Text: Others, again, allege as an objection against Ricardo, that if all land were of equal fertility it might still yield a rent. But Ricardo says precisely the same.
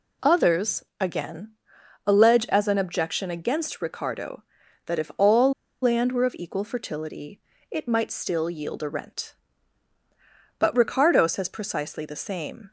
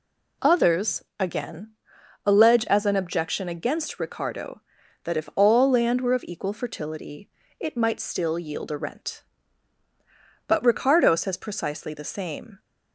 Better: second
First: pauses between "all" and "land"; slight; at 5.5 s; 0.29 s long // pauses between "fertility" and "it"; slight; at 7.4 s; 0.30 s long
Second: pauses between "fertility" and "it"; slight; at 7.2 s; 0.30 s long

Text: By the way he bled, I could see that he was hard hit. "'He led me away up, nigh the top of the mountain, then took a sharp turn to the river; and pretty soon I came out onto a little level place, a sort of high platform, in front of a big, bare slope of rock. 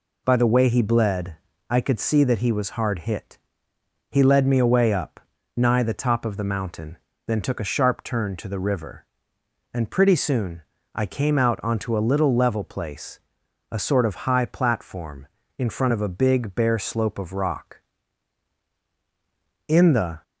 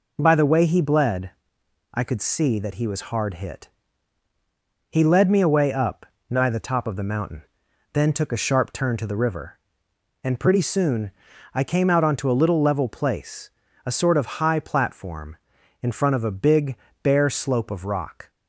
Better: second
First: pauses between "soon" and "I"; slight; at 10.6 s; 0.32 s long // goes on to say "In the"; from 19.6 s on; 0.56 s long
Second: pauses between "soon" and "I"; at 11.1 s; 0.42 s long

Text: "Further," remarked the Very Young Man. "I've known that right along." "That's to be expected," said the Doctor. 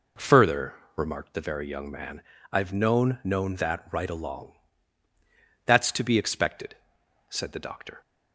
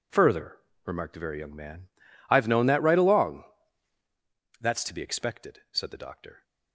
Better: second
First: says "known" twice; at 3.2 s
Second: none

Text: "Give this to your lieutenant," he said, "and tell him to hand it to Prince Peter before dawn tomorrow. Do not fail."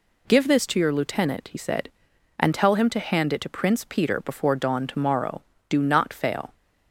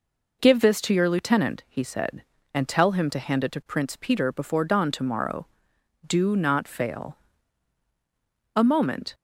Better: first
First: none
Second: goes on to say "A moment"; from 8.5 s on; 0.58 s long

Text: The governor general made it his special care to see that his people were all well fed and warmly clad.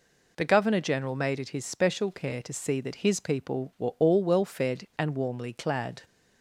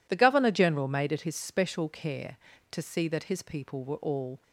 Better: first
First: none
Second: stops before "well fed and warmly clad"; at 4.4 s

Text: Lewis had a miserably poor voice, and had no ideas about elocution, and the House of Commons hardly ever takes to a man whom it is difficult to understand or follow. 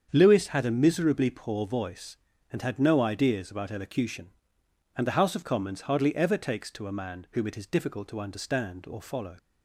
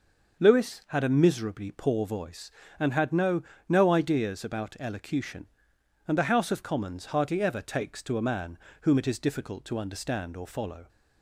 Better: first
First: starts louder than the rest; strong; until 1.1 s; 7.5 dB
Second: starts louder than the rest; noticeable; until 1.4 s; 6 dB // says "no" twice; at 3.6 s // pauses between "man" and "whom"; slight; at 8.5 s; 0.22 s long

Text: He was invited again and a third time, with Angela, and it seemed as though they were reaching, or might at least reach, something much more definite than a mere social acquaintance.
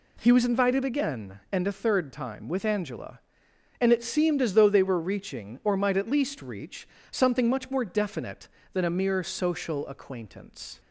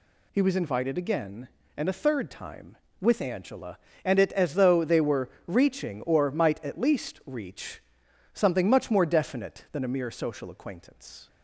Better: first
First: none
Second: skips "seemed"; at 4.3 s // pauses between "were" and "reaching"; slight; at 5.2 s; 0.18 s long

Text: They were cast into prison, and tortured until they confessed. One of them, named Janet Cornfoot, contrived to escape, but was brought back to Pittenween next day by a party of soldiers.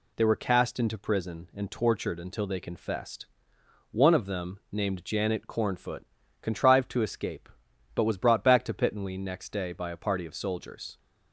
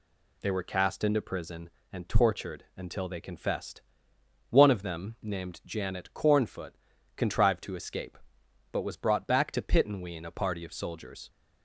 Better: first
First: none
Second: skips "next day by"; at 10.2 s

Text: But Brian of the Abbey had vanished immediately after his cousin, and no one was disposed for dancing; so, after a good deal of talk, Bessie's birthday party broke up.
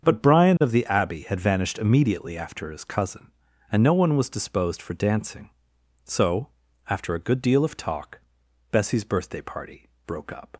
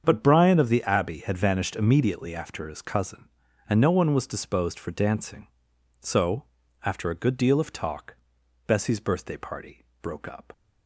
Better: neither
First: starts louder than the rest; strong; until 1.0 s; 7 dB // pauses between "party" and "broke"; slight; at 9.8 s; 0.16 s long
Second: starts louder than the rest; strong; until 1.0 s; 7 dB // pauses between "party" and "broke"; slight; at 9.8 s; 0.16 s long

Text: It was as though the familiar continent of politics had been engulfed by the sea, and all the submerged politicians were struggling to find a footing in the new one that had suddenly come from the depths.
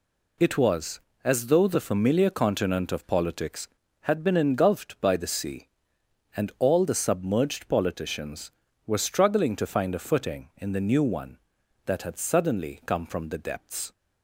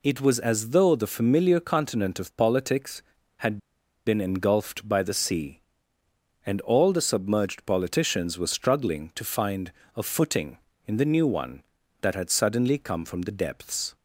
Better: first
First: none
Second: pauses between "had" and "been"; noticeable; at 3.5 s; 0.49 s long // pauses between "find" and "a"; slight; at 9.7 s; 0.24 s long

